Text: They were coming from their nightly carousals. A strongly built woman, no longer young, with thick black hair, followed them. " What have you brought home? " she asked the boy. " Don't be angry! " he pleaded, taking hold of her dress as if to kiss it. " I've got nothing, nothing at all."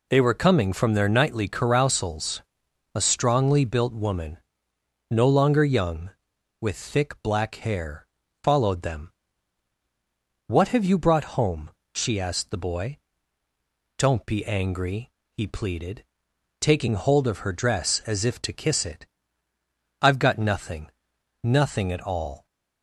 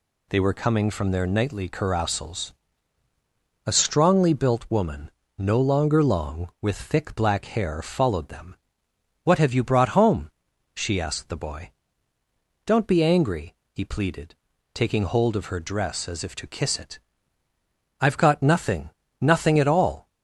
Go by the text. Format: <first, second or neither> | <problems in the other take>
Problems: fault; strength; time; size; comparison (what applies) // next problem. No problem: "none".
first | says "long" for "young"; at 6.0 s